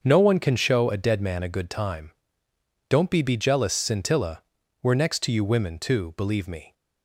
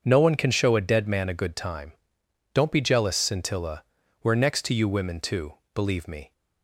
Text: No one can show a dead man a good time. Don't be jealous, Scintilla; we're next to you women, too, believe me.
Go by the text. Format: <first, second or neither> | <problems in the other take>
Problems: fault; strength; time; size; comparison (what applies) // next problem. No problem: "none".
second | starts louder than the rest; until 1.0 s; 6.5 dB; also in the second // says "be" twice; at 3.2 s